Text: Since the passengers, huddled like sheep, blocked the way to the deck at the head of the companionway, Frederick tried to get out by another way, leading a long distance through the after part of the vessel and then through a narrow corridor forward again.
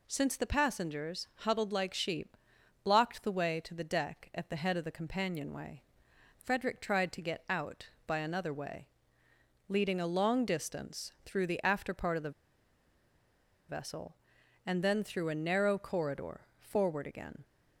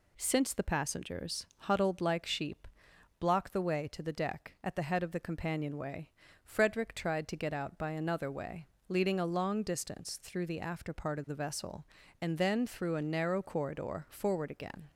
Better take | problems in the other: second | pauses between "the" and "vessel"; strong; at 12.3 s; 1.3 s long

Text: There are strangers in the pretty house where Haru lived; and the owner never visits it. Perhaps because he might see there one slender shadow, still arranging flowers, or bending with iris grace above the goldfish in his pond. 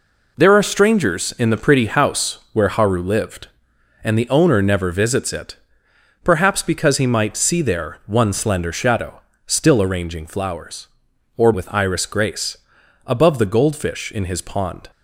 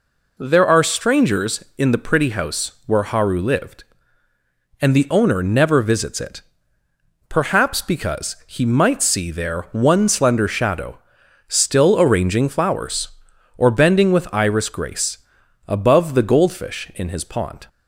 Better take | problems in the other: second | skips "bending"; at 11.5 s // pauses between "grace" and "above"; noticeable; at 12.5 s; 0.48 s long; noticeable in the second

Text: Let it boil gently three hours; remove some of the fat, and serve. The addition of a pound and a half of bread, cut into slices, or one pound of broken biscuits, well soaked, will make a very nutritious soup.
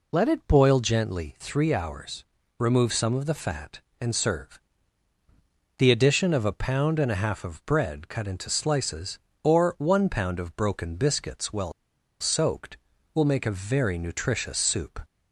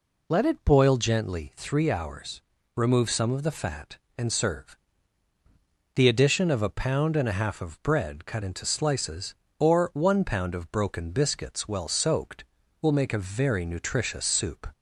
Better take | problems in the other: second | pauses between "well" and "soaked"; noticeable; at 11.7 s; 0.48 s long

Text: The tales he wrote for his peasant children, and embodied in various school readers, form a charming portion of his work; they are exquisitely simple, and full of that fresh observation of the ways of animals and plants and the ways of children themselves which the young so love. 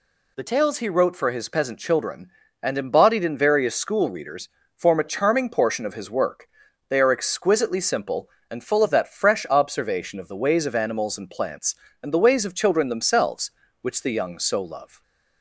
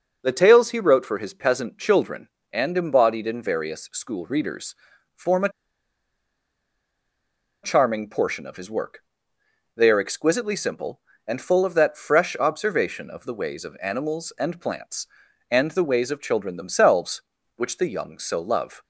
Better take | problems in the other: first | starts louder than the rest; noticeable; until 1.2 s; 6 dB // pauses between "a" and "charming"; strong; at 5.4 s; 2.1 s long

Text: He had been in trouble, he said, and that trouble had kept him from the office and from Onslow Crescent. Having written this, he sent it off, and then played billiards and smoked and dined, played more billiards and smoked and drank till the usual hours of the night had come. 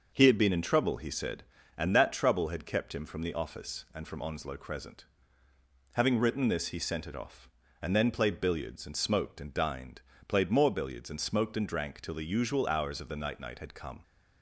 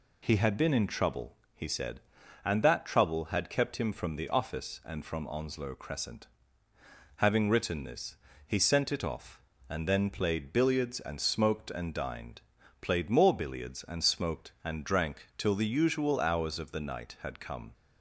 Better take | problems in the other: second | says "night" twice; at 13.3 s

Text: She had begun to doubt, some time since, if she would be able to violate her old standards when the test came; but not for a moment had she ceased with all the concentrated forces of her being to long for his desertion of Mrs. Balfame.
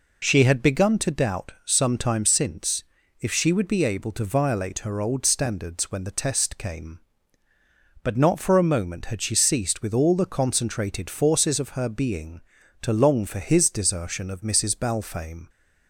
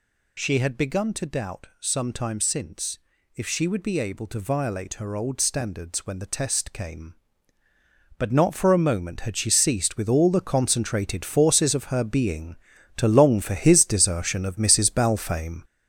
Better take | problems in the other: first | gets louder; strong; throughout; 7 dB

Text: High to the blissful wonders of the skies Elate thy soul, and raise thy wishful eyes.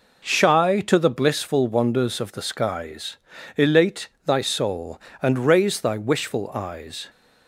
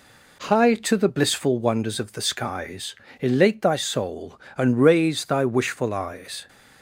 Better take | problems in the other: second | says "Shy" for "High"; at 0.2 s // pauses between "skies" and "Elate"; at 3.1 s; 0.39 s long; slight in the second // pauses between "Elate" and "thy"; slight; at 4.0 s; 0.18 s long

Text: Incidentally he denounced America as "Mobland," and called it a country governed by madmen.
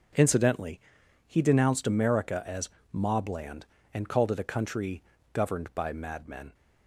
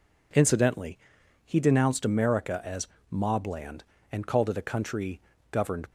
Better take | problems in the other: first | pauses between "Incidentally" and "he"; noticeable; at 0.9 s; 0.46 s long; noticeable in the first // pauses between "as" and "Mobland"; slight; at 2.8 s; 0.24 s long; slight in the first // pauses between "country" and "governed"; slight; at 5.1 s; 0.32 s long; slight in the first // stops before "by madmen"; at 5.8 s

